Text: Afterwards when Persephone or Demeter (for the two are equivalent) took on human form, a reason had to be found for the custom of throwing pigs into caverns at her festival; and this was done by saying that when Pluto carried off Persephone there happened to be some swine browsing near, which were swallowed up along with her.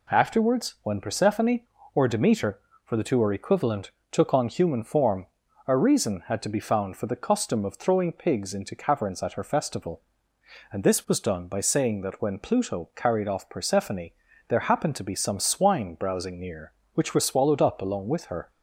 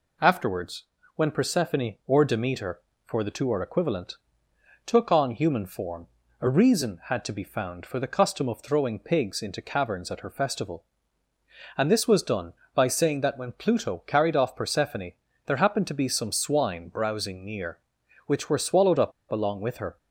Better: first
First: pauses between "Persephone" and "there"; at 14.0 s; 0.38 s long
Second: pauses between "Afterwards" and "when"; slight; at 0.8 s; 0.32 s long // pauses between "Persephone" and "there"; slight; at 15.1 s; 0.34 s long // pauses between "up" and "along"; slight; at 19.1 s; 0.18 s long

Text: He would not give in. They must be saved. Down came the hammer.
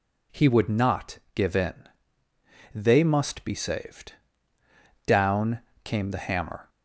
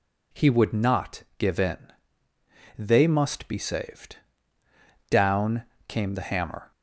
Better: neither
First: pauses between "not" and "give"; slight; at 1.1 s; 0.16 s long // pauses between "Down" and "came"; slight; at 5.6 s; 0.24 s long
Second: pauses between "not" and "give"; slight; at 1.2 s; 0.15 s long // pauses between "Down" and "came"; slight; at 5.6 s; 0.24 s long

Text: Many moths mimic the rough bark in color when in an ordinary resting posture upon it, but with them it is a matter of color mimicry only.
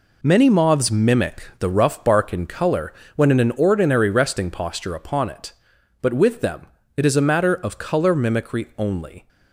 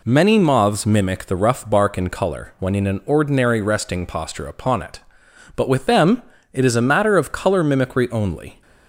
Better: second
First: gets quieter; strong; throughout; 9 dB // pauses between "color" and "when"; slight; at 2.9 s; 0.22 s long // pauses between "them" and "it"; slight; at 6.6 s; 0.30 s long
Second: pauses between "them" and "it"; slight; at 6.2 s; 0.30 s long

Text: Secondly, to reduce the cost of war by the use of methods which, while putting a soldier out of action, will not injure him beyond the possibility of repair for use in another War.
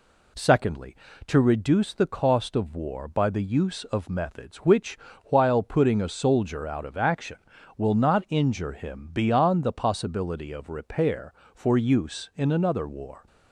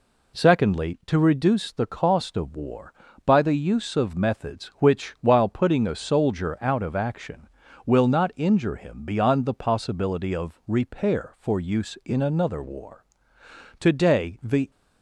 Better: first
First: none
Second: goes on to say "Today the"; noticeable; from 13.7 s on; 0.92 s long

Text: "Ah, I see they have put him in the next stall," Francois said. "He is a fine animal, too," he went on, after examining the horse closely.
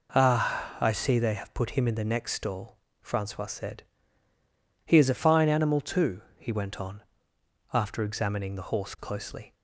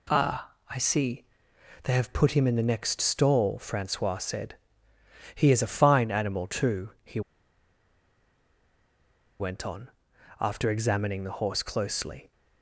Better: first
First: none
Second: pauses between "see" and "they"; noticeable; at 1.2 s; 0.60 s long // pauses between "he" and "went"; strong; at 7.2 s; 2.1 s long

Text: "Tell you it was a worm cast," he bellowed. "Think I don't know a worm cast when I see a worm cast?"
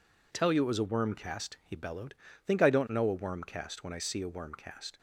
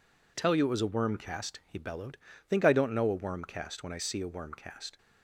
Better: neither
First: none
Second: none

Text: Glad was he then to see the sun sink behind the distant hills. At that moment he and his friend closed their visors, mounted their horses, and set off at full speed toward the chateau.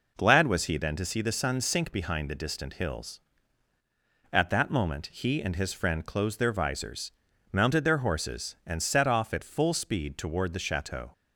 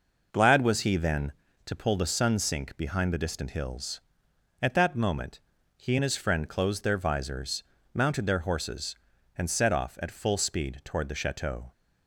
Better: first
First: none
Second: says "pull" for "see"; at 1.7 s // pauses between "moment" and "he"; slight; at 5.4 s; 0.36 s long

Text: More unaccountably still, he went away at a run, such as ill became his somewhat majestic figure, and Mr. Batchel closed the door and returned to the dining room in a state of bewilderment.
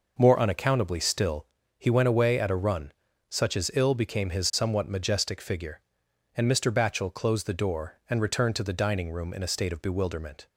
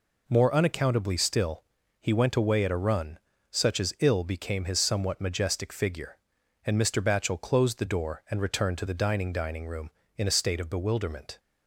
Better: first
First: none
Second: says "dining" twice; at 9.3 s

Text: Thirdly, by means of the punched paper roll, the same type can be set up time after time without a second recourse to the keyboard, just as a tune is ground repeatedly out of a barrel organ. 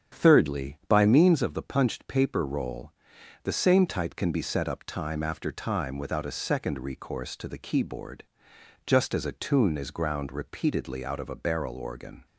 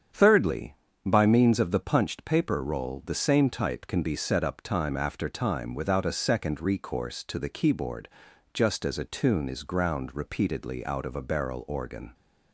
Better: neither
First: starts louder than the rest; strong; until 1.2 s; 8.5 dB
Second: starts louder than the rest; strong; until 1.4 s; 8 dB

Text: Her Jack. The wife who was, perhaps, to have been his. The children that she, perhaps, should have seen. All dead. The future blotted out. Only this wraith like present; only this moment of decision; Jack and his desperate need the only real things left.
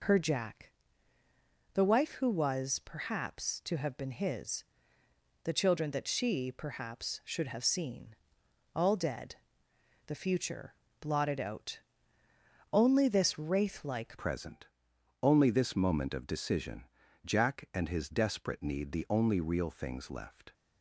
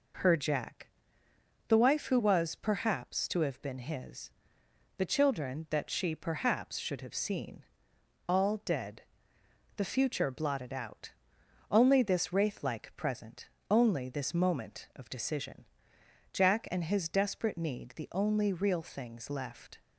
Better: second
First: pauses between "future" and "blotted"; slight; at 10.7 s; 0.24 s long // changes voice at "present"; from 14.1 s on; 6.4 s long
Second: none

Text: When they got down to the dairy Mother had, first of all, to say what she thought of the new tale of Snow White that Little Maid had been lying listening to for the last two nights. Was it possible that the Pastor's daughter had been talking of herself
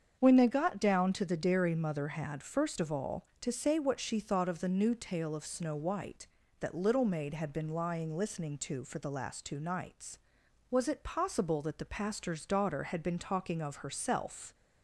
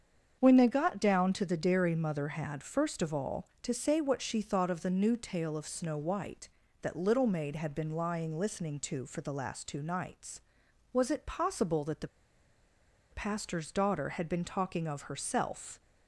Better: first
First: starts louder than the rest; strong; until 1.2 s; 7 dB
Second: starts louder than the rest; strong; until 1.4 s; 7 dB // pauses between "the" and "Pastor's"; at 12.0 s; 1.0 s long

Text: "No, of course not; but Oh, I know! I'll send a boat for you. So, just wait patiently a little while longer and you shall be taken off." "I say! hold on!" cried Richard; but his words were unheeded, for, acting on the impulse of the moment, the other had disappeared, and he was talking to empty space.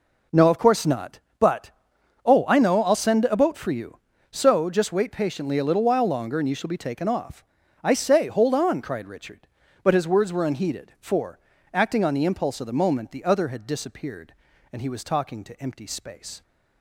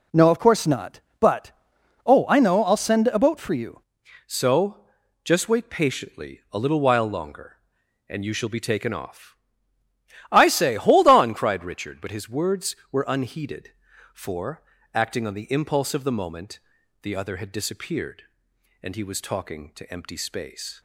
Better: first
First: pauses between "but" and "Oh"; noticeable; at 1.7 s; 0.54 s long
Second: pauses between "but" and "Oh"; noticeable; at 1.5 s; 0.54 s long // changes voice at "So"; from 4.2 s on; 16.6 s long

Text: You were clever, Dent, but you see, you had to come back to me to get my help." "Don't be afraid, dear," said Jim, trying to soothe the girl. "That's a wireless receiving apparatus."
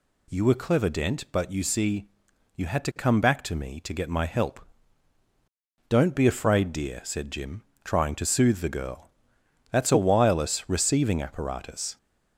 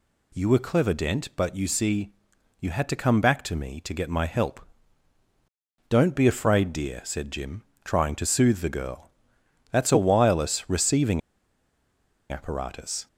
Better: first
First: none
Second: pauses between "receiving" and "apparatus"; at 11.2 s; 1.1 s long

